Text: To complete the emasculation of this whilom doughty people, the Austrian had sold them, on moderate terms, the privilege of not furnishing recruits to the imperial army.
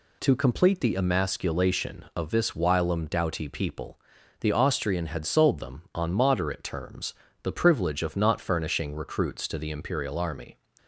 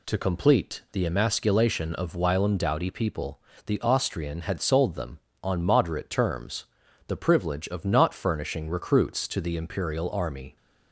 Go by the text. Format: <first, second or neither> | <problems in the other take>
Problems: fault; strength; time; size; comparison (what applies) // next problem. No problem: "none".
first | skips "this"; at 2.1 s